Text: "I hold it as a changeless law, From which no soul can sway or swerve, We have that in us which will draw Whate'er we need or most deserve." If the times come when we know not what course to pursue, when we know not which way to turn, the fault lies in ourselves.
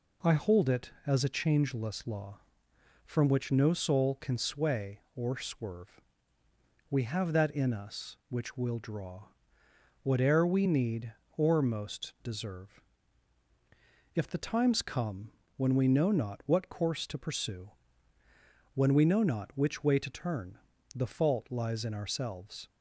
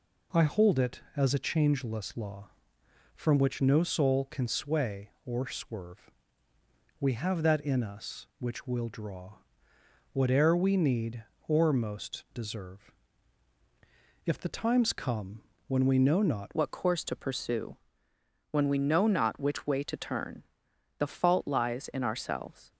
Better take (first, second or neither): first